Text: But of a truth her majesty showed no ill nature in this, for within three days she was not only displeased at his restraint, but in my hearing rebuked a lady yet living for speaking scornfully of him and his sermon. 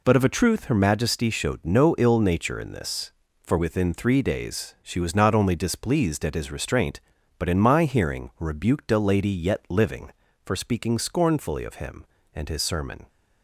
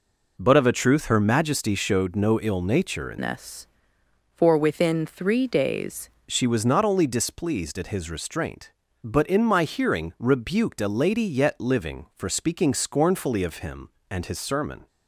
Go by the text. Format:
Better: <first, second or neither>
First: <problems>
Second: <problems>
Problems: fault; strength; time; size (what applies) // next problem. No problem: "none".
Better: first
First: none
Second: changes voice from "this" to "days"; from 3.1 to 6.0 s; 2.9 s long